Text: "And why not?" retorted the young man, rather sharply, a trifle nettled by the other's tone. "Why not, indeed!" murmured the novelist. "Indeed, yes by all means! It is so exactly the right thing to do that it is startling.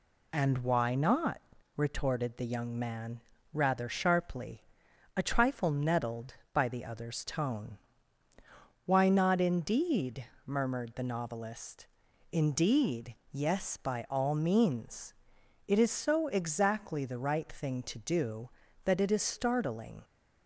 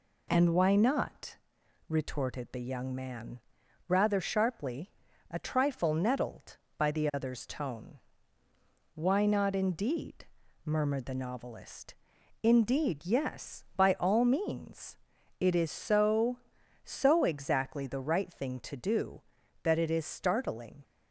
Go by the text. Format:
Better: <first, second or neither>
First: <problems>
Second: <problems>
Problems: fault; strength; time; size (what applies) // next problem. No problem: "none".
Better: first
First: none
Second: says "so" twice; at 16.8 s